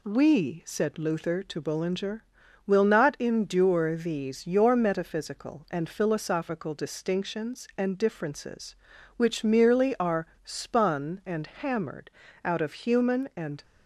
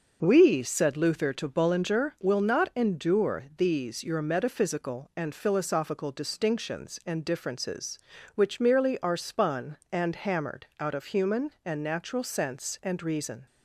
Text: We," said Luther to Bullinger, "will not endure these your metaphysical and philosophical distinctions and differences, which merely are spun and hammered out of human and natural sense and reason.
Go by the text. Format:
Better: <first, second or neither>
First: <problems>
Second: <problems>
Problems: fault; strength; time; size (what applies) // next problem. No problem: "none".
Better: second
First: pauses between "are" and "spun"; slight; at 10.2 s; 0.17 s long // pauses between "hammered" and "out"; slight; at 12.1 s; 0.32 s long // stops before "natural sense and reason"; at 13.6 s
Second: none